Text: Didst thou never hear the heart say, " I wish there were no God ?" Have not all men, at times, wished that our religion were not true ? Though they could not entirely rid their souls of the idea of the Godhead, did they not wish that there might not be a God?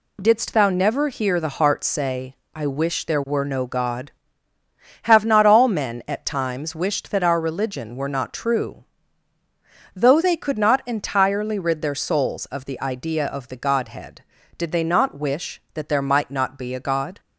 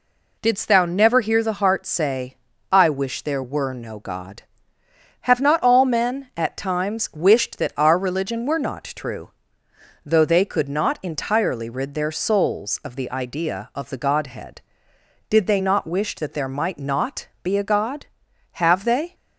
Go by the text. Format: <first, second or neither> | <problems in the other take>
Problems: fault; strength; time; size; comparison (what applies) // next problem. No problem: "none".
first | pauses between "not" and "be"; slight; at 17.2 s; 0.16 s long // goes on to say "Have they"; from 18.5 s on; 0.60 s long